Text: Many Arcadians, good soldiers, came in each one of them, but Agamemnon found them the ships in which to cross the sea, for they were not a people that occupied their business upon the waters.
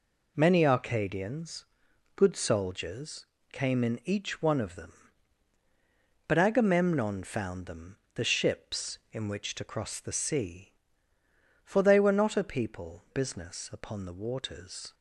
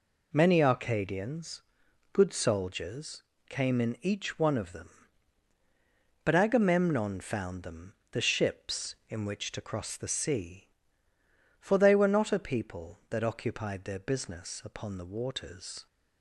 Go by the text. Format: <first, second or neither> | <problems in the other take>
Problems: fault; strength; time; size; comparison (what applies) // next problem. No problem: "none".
second | pauses between "them" and "the"; slight; at 7.9 s; 0.18 s long; slight in the second // skips "that occupied their"; at 13.0 s